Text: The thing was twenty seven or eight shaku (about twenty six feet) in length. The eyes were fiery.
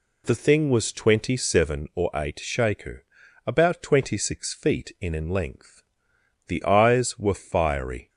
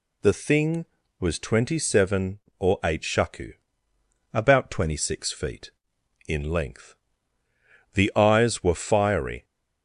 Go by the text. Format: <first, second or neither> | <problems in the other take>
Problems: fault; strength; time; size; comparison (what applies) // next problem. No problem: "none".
second | says "in" twice; at 5.1 s